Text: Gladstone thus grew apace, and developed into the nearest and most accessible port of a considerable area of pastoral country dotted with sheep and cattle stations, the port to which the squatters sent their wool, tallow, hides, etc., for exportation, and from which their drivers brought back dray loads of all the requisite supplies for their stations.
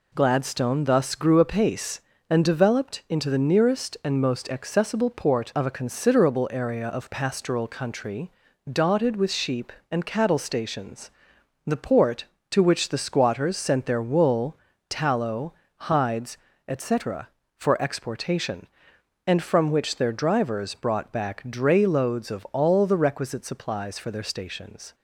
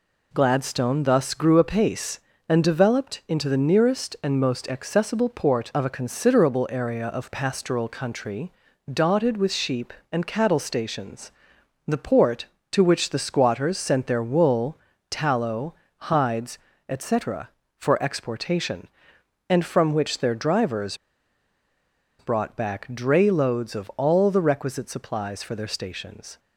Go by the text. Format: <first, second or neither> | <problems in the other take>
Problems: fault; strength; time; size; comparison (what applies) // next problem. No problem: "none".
first | pauses between "country" and "dotted"; at 8.5 s; 0.38 s long; also in the first // pauses between "drivers" and "brought"; at 20.9 s; 1.2 s long